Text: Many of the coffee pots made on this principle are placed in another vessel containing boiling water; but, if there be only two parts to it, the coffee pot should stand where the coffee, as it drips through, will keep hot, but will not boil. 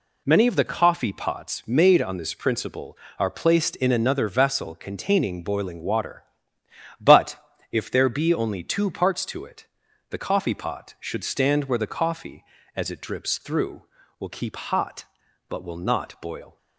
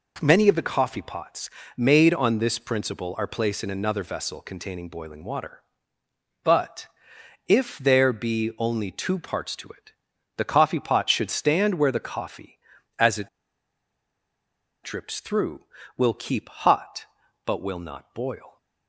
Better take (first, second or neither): first